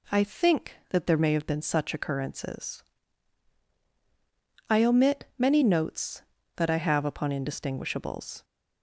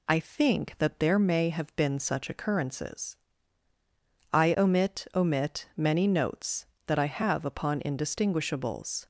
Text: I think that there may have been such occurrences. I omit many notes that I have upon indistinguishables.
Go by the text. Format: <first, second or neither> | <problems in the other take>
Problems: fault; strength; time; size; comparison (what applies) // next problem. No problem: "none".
first | says "omit" twice; at 5.1 s